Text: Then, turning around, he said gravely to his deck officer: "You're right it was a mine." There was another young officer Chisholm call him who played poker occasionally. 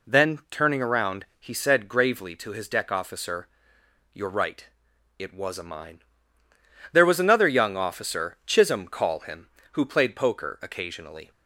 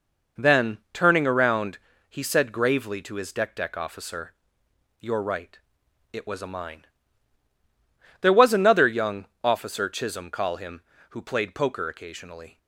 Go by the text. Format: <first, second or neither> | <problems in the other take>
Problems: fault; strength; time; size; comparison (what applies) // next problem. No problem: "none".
first | says "deck" twice; at 3.5 s // pauses between "right" and "it"; noticeable; at 5.5 s; 0.52 s long; noticeable in the first // pauses between "young" and "officer"; slight; at 9.2 s; 0.18 s long